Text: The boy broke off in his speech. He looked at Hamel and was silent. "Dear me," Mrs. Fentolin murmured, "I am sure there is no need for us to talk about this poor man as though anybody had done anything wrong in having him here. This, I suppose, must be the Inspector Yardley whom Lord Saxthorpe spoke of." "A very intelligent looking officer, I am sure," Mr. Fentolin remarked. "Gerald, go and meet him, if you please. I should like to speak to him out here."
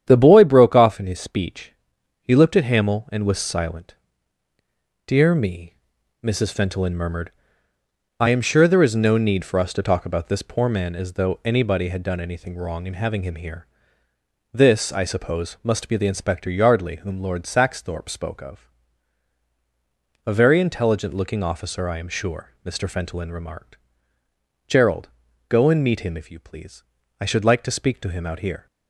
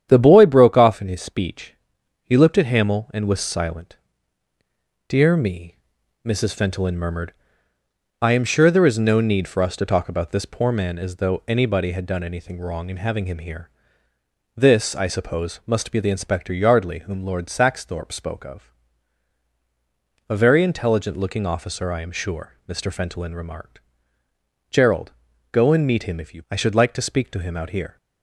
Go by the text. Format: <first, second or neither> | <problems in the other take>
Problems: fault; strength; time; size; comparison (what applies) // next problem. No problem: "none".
first | starts louder than the rest; strong; until 1.1 s; 9.5 dB; strong in the first // skips "please"; at 26.4 s